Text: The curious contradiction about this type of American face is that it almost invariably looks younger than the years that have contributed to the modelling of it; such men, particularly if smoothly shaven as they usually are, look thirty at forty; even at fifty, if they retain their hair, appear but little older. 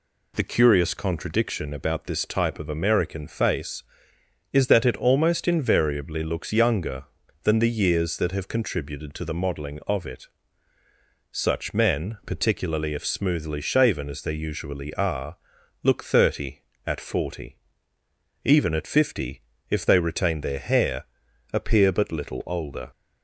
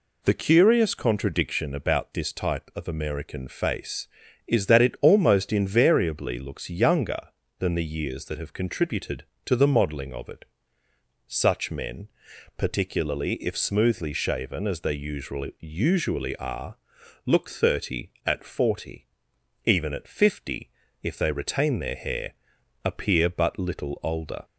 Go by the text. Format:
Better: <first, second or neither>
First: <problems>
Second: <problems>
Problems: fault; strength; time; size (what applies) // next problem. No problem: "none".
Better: first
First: none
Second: says "usually" twice; at 15.5 s